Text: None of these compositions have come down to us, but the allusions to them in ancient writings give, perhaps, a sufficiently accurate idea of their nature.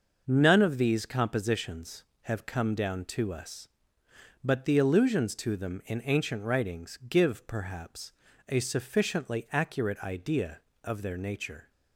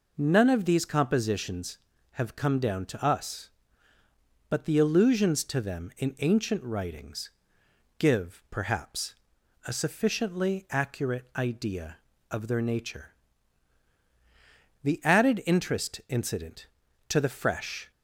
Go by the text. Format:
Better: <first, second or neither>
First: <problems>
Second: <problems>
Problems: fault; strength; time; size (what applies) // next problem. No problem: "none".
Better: first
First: none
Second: pauses between "writings" and "give"; noticeable; at 7.3 s; 0.68 s long // goes on to say "The added interest incident to the fresh"; strong; from 14.8 s on; 3.0 s long